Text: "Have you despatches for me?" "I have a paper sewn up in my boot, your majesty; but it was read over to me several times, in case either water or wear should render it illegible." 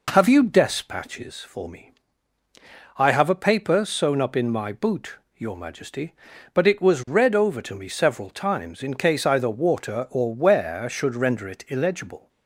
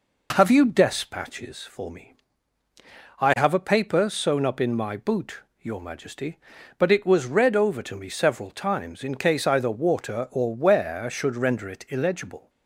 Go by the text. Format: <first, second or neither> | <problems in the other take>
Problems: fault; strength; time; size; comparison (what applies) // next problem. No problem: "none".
neither | none